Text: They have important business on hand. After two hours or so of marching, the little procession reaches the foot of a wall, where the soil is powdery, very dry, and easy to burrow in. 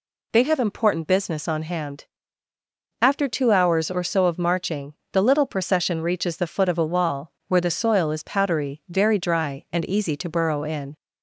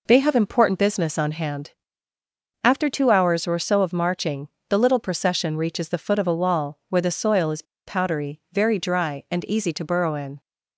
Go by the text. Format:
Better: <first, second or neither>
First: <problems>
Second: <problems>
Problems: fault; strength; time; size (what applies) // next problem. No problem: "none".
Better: first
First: none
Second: pauses between "is" and "powdery"; slight; at 7.6 s; 0.23 s long